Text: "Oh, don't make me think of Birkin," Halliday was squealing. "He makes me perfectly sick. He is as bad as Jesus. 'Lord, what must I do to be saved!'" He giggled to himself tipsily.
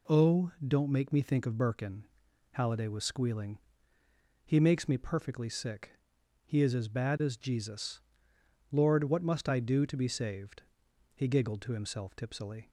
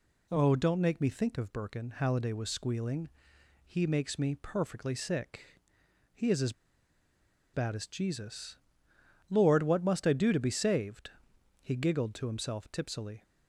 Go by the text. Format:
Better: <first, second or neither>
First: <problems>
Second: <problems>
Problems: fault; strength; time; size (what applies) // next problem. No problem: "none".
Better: first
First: none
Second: pauses between "as" and "bad"; at 6.5 s; 1.0 s long